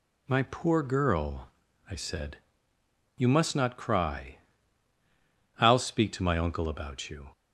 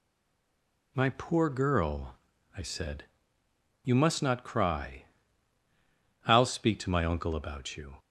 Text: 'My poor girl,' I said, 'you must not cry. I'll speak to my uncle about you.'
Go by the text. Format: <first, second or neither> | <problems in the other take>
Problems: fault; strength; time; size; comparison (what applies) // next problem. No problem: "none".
first | stays silent before the first word; slight; until 0.9 s; 0.9 s long